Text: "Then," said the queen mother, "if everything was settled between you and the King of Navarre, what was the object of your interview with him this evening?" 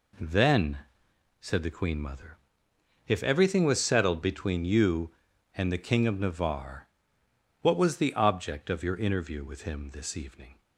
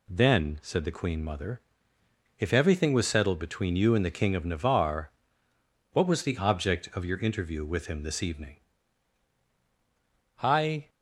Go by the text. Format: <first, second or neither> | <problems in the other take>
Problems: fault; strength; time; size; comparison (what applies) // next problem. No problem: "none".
first | goes on to say "I"; slight; from 10.4 s on; 0.46 s long